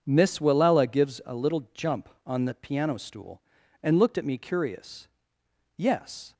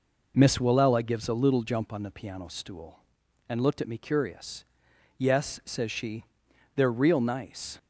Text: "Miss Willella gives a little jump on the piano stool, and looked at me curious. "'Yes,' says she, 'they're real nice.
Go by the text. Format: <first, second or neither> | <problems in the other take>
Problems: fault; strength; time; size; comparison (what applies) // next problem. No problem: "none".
second | stops before "says she they're real nice"; at 6.3 s